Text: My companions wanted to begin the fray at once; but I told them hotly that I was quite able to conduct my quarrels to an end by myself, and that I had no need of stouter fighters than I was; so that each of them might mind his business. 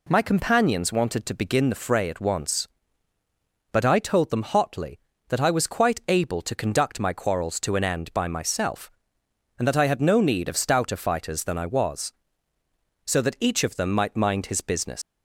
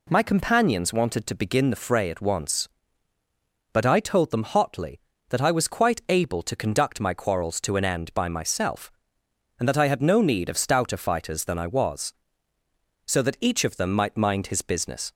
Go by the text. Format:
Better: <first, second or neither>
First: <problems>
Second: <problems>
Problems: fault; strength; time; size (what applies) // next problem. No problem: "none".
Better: second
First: leaves "business" unfinished; at 15.0 s; 95 ms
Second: none